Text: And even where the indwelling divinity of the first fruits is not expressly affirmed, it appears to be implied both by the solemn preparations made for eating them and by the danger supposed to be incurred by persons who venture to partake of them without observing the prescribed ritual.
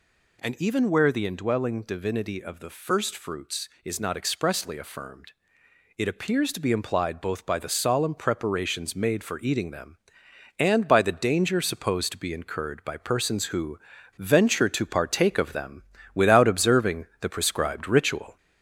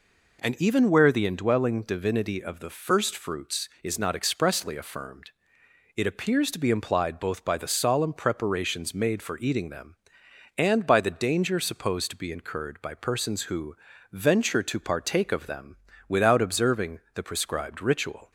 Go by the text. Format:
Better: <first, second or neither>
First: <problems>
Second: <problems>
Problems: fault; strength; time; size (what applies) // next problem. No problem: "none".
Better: second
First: gets louder; throughout; 3.5 dB // pauses between "who" and "venture"; at 13.7 s; 0.39 s long // pauses between "them" and "without"; slight; at 15.8 s; 0.32 s long // pauses between "observing" and "the"; slight; at 17.0 s; 0.16 s long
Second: pauses between "who" and "venture"; slight; at 13.7 s; 0.36 s long // pauses between "them" and "without"; slight; at 15.7 s; 0.32 s long // pauses between "observing" and "the"; slight; at 16.9 s; 0.16 s long